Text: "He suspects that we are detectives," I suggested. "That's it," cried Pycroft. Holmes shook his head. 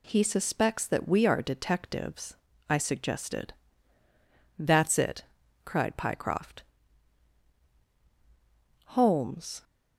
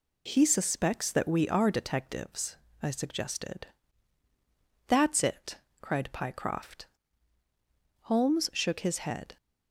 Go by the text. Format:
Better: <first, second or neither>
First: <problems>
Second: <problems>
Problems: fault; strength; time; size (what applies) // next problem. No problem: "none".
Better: second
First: stops before "shook his head"; at 9.6 s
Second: none